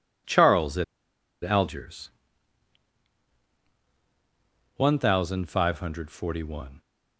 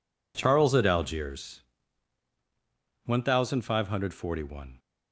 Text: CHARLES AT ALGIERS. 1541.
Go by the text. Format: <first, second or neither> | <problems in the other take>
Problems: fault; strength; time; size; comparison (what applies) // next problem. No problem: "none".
second | pauses between "AT" and "ALGIERS"; noticeable; at 0.8 s; 0.59 s long